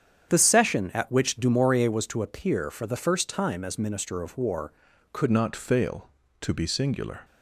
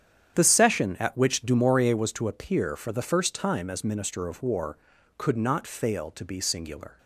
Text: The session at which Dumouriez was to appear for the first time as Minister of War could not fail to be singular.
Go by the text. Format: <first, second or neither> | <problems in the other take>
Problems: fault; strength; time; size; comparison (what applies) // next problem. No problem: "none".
second | starts louder than the rest; strong; until 1.3 s; 8.5 dB; strong in the second // changes voice at "not"; from 5.2 s on; 2.0 s long